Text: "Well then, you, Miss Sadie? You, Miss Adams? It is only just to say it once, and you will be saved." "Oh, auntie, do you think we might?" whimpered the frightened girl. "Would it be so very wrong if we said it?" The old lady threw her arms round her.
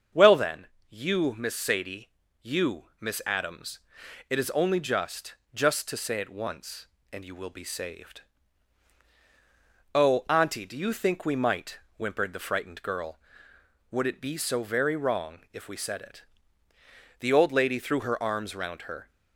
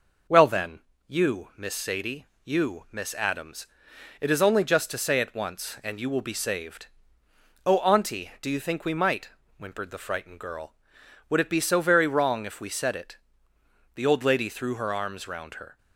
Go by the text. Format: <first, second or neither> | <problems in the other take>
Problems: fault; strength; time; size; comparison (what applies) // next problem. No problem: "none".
second | starts louder than the rest; until 1.3 s; 7 dB // says "just" twice; at 5.5 s